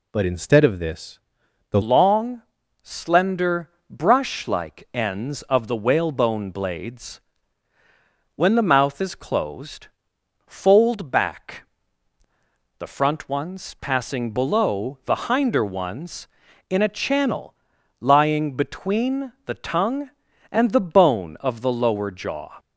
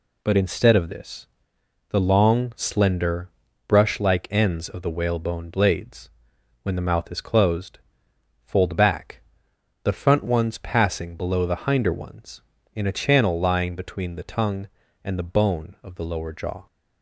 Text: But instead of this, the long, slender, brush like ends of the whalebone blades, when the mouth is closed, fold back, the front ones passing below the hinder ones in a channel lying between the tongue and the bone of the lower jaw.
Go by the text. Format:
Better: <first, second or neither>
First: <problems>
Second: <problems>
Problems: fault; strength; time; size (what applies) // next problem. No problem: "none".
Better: second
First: changes voice at "long"; from 1.8 s on; 20.7 s long // pauses between "channel" and "lying"; noticeable; at 17.5 s; 0.46 s long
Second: none